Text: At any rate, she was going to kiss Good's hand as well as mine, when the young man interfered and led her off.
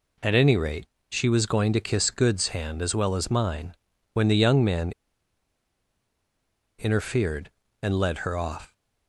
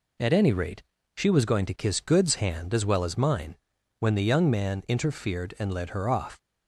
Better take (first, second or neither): second